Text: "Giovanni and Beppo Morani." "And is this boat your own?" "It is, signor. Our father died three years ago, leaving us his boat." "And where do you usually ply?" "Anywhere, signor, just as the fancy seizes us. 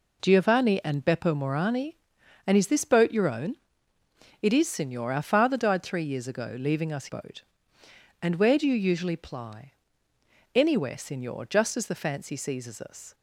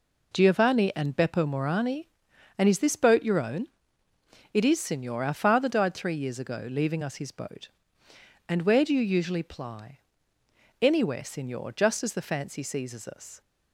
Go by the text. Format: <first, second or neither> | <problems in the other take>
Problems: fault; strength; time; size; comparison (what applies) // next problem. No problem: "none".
second | skips "his"; at 7.0 s